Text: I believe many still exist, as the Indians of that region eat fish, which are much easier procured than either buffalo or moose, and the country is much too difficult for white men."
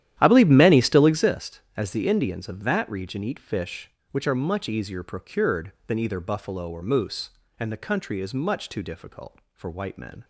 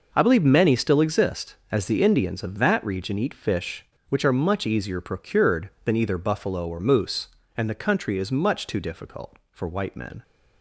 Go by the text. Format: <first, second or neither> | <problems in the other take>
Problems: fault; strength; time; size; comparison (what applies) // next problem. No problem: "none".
second | starts louder than the rest; strong; until 1.4 s; 11.5 dB